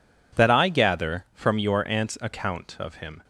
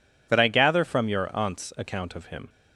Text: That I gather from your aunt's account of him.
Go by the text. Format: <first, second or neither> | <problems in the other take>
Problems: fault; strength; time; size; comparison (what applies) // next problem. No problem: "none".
neither | none